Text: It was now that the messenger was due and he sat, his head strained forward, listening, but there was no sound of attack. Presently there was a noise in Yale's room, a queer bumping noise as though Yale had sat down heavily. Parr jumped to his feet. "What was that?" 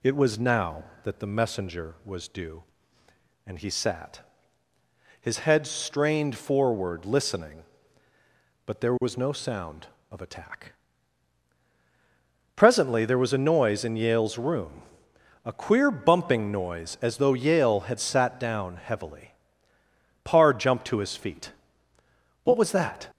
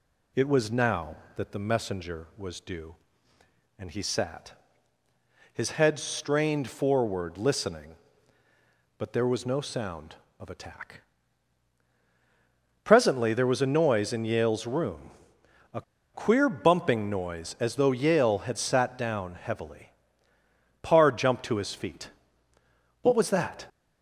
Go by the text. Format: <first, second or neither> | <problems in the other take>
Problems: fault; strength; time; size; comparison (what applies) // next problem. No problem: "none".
first | pauses between "a" and "queer"; slight; at 15.8 s; 0.32 s long